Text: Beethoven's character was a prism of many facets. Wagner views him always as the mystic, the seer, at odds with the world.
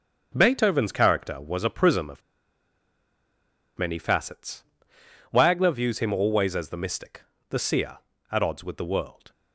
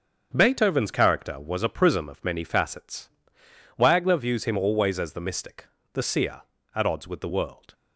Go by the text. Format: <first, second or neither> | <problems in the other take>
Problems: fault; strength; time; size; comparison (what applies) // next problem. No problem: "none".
second | starts louder than the rest; until 1.3 s; 6.5 dB; also in the second // pauses between "of" and "many"; strong; at 2.2 s; 1.5 s long